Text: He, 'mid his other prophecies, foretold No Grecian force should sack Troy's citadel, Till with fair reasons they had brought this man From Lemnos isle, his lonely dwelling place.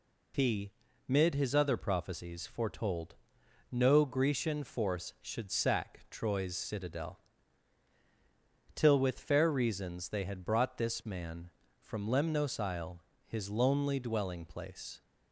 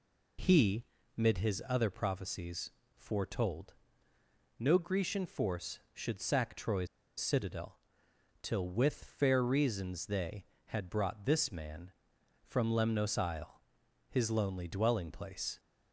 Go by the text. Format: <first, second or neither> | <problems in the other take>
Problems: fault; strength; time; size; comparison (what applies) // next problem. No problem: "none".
first | pauses between "foretold" and "No"; noticeable; at 3.7 s; 0.84 s long; noticeable in the first // pauses between "Troy's" and "citadel"; slight; at 6.8 s; 0.31 s long